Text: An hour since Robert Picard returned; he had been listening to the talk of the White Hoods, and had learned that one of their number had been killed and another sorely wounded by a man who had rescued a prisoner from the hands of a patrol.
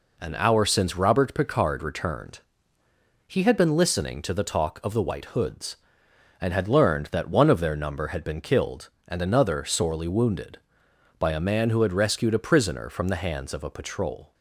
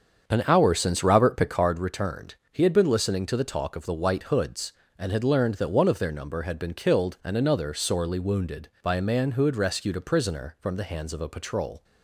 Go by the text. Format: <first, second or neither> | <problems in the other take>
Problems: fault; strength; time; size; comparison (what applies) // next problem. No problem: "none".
first | starts louder than the rest; until 1.7 s; 7 dB